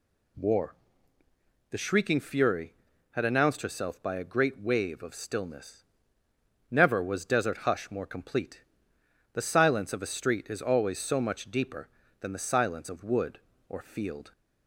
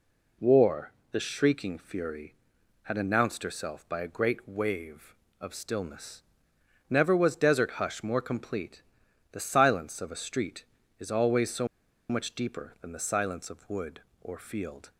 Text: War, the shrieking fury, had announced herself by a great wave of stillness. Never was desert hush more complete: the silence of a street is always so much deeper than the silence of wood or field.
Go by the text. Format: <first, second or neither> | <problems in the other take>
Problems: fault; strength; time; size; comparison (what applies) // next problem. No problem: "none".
first | pauses between "so" and "much"; at 11.6 s; 0.44 s long